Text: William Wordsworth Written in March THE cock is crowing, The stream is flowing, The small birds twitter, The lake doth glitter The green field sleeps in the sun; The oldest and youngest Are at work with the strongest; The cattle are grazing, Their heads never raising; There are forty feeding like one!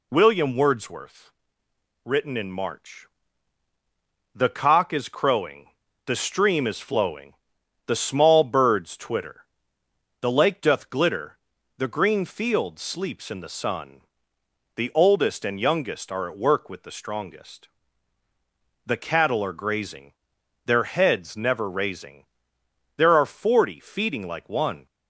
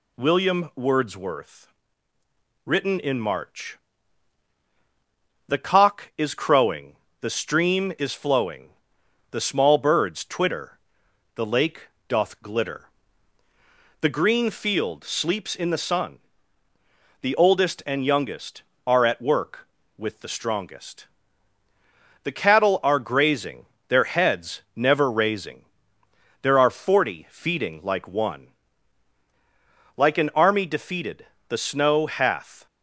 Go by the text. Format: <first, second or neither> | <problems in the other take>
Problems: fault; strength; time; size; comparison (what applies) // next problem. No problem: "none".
first | pauses between "Wordsworth" and "Written"; noticeable; at 1.7 s; 0.94 s long; noticeable in the first // pauses between "March" and "THE"; strong; at 3.7 s; 1.7 s long; strong in the first // pauses between "lake" and "doth"; slight; at 11.8 s; 0.20 s long // pauses between "glitter" and "The"; at 12.8 s; 1.2 s long; also in the first // goes on to say "Like an army defeated The snow hath"; strong; from 29.9 s on; 2.7 s long